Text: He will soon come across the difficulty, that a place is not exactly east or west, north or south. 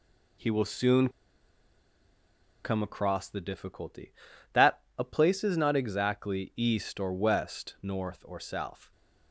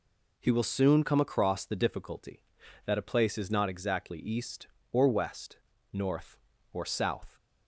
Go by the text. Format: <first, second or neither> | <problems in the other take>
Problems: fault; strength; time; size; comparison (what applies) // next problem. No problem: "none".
second | pauses between "soon" and "come"; strong; at 1.0 s; 1.5 s long // pauses between "that" and "a"; slight; at 4.7 s; 0.18 s long